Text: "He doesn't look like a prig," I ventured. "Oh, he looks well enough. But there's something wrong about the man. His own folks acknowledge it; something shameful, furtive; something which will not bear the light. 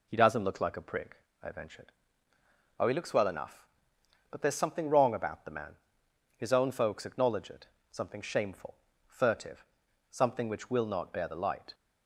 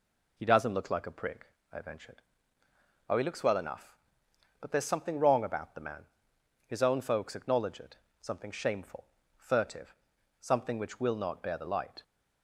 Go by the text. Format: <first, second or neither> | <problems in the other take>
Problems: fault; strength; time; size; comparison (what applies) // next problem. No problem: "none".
neither | none